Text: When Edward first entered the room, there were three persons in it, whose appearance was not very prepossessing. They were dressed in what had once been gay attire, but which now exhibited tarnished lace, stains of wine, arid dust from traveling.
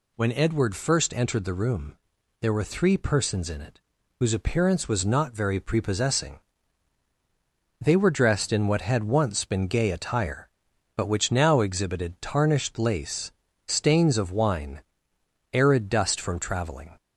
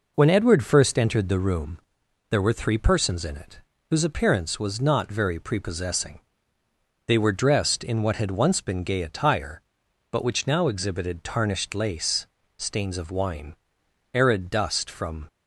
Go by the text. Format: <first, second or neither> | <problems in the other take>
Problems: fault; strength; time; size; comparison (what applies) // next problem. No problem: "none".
first | stops before "traveling"; at 15.2 s